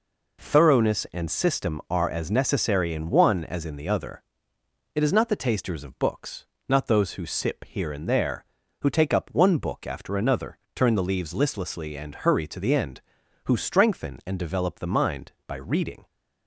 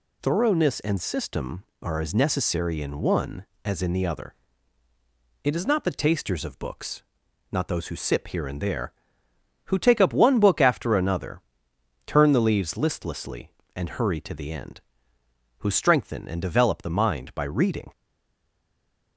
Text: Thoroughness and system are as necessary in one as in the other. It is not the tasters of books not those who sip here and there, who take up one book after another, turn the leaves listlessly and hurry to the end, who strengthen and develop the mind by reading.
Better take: first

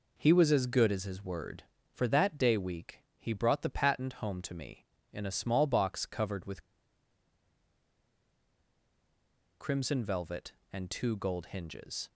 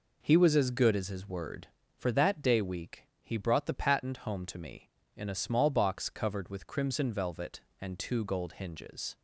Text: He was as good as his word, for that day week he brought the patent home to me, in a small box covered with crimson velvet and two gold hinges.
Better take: second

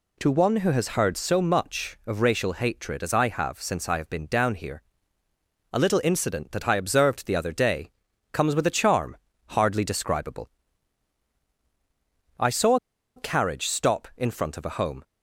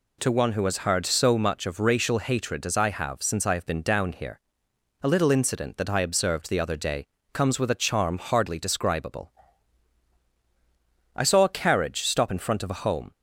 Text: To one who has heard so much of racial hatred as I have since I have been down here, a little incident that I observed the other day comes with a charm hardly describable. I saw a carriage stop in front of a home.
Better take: second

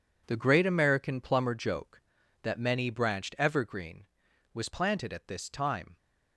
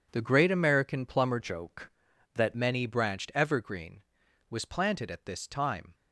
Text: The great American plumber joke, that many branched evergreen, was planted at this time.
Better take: first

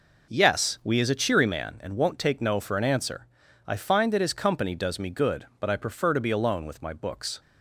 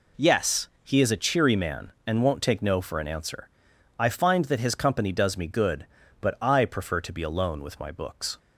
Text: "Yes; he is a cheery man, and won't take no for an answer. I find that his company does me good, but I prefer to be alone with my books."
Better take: second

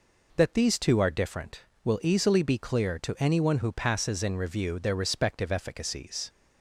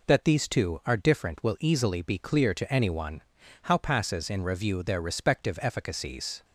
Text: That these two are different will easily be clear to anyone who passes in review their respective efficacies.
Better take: first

